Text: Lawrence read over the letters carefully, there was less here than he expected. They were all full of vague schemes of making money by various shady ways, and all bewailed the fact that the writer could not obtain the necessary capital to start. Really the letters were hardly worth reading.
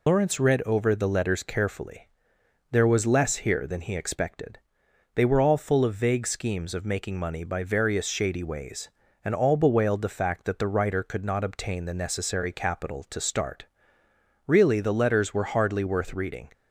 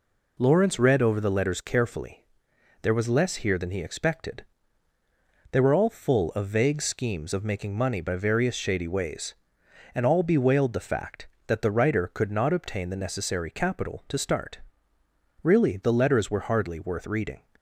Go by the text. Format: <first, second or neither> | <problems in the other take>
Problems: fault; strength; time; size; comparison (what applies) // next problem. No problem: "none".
second | loses the start of "Lawrence"; at 0.0 s; 70 ms